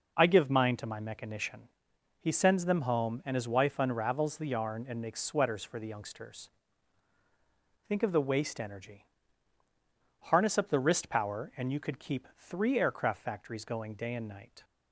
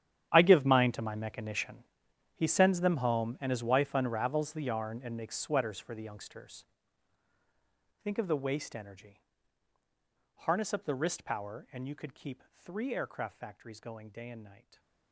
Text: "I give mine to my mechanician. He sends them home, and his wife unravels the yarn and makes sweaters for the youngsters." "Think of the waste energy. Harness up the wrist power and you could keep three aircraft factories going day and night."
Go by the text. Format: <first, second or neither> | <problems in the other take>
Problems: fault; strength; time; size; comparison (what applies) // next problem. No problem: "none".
first | gets quieter; strong; throughout; 16.5 dB // stays silent after the last word; slight; from 14.5 s on; 0.6 s long